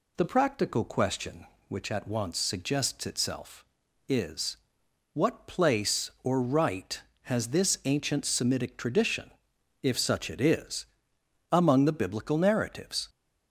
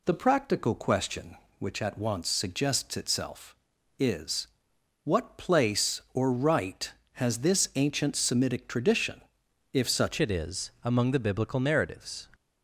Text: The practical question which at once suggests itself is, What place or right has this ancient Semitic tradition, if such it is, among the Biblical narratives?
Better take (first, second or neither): first